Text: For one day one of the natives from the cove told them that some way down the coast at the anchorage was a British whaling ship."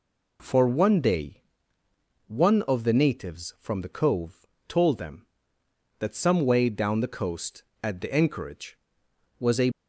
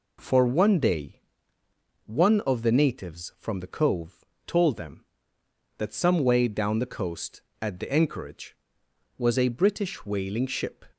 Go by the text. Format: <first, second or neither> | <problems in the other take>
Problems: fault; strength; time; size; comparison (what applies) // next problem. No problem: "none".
second | pauses between "day" and "one"; noticeable; at 1.4 s; 0.84 s long; noticeable in the second // pauses between "cove" and "told"; slight; at 4.4 s; 0.20 s long; slight in the second // stops before "British whaling ship"; at 9.7 s